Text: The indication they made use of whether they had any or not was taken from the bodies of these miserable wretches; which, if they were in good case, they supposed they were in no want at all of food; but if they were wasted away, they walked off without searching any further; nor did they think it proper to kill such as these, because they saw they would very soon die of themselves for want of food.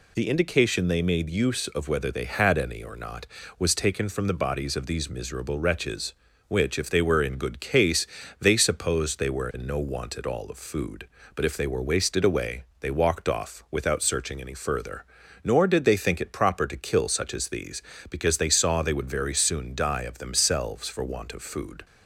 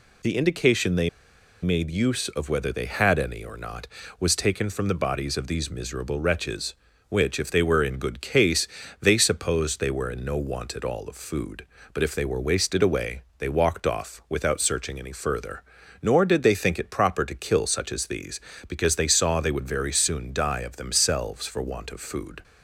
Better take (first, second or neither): first